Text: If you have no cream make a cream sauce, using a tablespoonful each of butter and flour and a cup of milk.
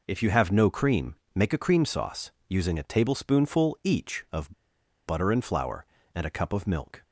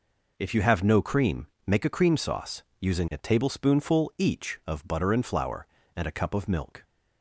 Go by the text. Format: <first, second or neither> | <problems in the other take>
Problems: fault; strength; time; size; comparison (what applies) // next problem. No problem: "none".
second | pauses between "cream" and "make"; slight; at 1.1 s; 0.18 s long; slight in the second // pauses between "of" and "butter"; noticeable; at 4.5 s; 0.56 s long